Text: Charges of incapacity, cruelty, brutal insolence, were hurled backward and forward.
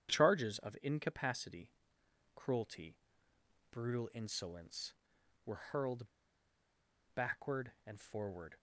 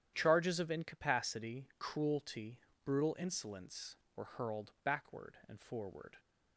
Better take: second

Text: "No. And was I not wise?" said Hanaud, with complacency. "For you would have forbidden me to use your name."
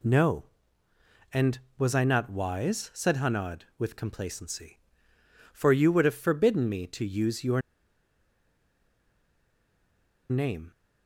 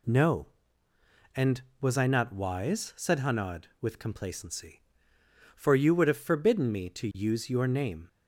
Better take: second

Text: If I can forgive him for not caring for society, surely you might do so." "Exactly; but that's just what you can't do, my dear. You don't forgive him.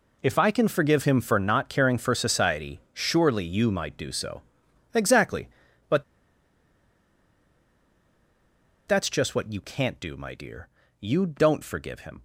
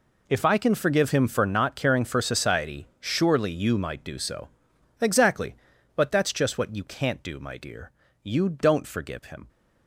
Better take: second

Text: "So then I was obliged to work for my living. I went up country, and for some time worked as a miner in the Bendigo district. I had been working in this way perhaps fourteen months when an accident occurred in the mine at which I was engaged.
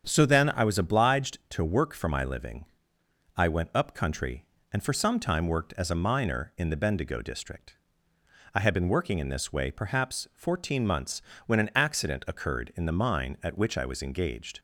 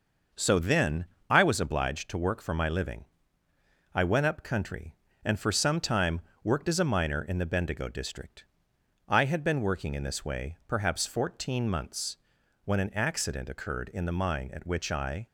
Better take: first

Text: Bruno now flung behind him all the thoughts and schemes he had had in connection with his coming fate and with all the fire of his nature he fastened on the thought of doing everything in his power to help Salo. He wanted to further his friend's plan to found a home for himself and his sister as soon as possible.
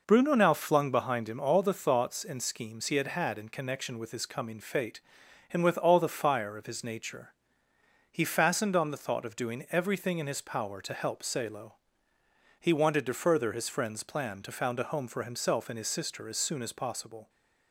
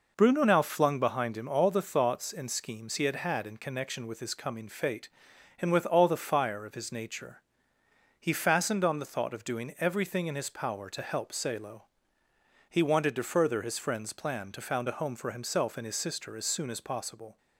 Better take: neither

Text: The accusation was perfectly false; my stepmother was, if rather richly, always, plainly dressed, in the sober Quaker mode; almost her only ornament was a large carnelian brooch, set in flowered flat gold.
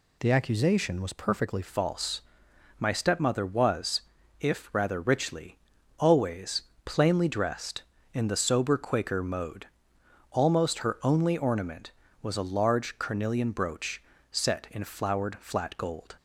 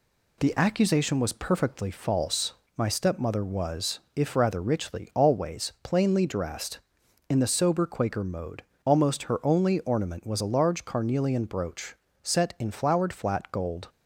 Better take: second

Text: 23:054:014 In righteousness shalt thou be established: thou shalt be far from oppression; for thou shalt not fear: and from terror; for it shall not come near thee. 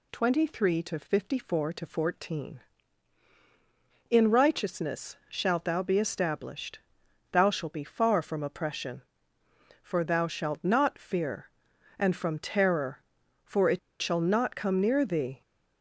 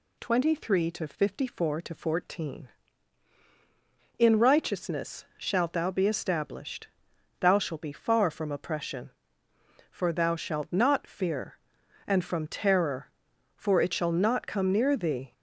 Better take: second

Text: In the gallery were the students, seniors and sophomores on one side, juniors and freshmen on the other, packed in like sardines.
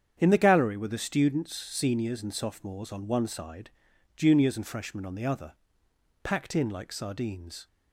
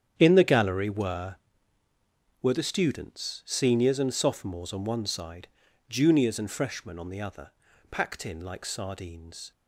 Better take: first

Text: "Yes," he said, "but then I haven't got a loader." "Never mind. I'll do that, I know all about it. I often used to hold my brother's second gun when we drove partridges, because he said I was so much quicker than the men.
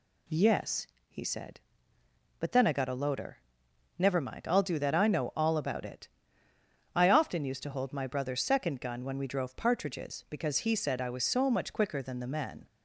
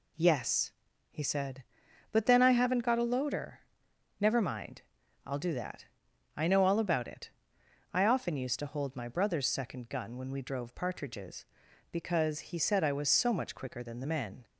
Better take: second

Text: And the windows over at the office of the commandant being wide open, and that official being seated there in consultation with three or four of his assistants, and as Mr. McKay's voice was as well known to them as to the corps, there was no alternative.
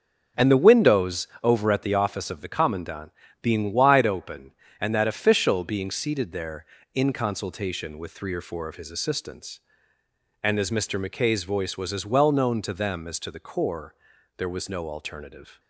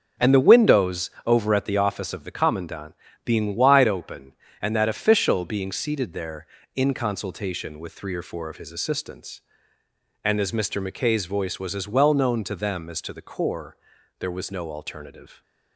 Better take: neither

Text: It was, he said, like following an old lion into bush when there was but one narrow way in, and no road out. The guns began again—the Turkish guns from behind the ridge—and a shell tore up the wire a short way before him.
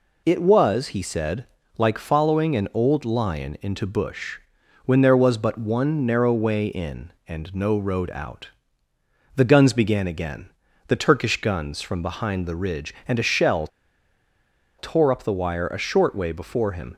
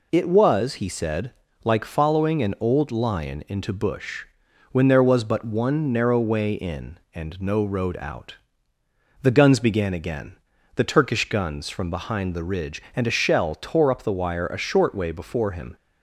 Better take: second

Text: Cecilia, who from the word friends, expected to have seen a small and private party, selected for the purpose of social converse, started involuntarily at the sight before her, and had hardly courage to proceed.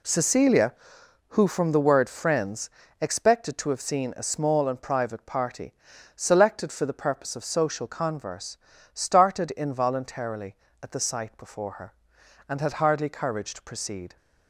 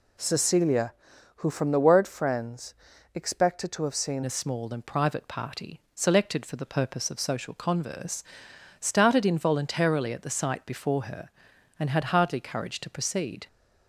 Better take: first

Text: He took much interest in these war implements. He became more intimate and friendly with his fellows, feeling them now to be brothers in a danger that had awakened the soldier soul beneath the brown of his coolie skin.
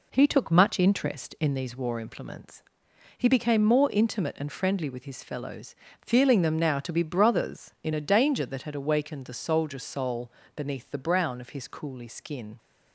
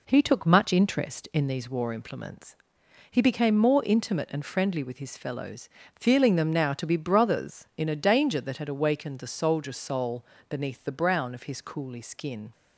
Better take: neither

